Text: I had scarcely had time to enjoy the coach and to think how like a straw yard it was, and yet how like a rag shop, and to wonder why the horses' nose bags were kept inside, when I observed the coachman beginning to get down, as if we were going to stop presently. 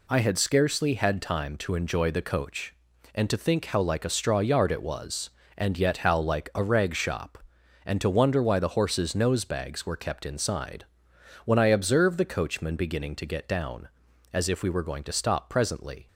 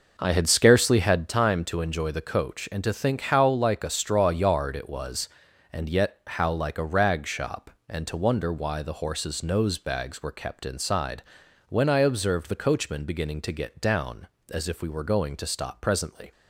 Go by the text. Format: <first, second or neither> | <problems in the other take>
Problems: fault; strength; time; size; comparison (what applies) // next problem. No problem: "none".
first | starts louder than the rest; noticeable; until 1.3 s; 5.5 dB